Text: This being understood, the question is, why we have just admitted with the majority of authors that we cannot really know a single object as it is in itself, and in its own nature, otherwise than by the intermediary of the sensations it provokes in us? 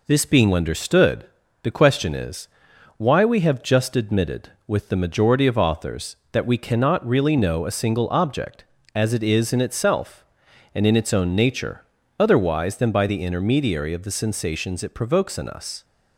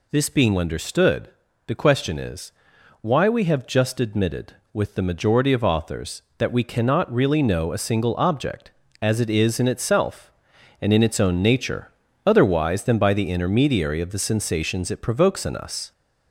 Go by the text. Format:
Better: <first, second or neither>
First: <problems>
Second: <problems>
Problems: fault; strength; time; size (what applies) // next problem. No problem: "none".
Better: first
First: none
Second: gets louder; slight; throughout; 3 dB